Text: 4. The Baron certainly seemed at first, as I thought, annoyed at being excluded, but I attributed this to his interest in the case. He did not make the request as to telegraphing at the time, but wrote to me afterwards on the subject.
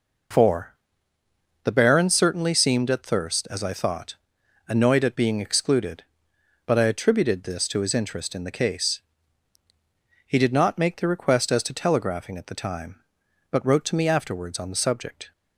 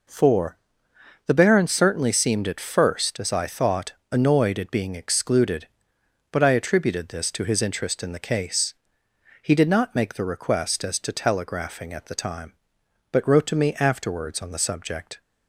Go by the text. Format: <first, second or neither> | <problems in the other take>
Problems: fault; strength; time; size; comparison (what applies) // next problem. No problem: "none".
second | says "thirst" for "first"; at 3.0 s